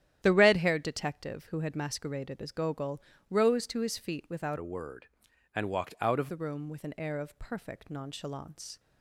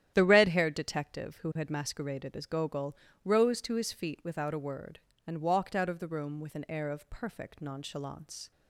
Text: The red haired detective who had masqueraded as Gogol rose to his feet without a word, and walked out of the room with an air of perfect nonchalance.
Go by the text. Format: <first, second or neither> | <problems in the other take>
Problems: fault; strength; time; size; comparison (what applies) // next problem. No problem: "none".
second | starts louder than the rest; strong; until 1.2 s; 11.5 dB; strong in the second // pauses between "Gogol" and "rose"; slight; at 2.9 s; 0.30 s long; slight in the second // changes voice from "a" to "of"; from 4.5 to 6.2 s; 1.7 s long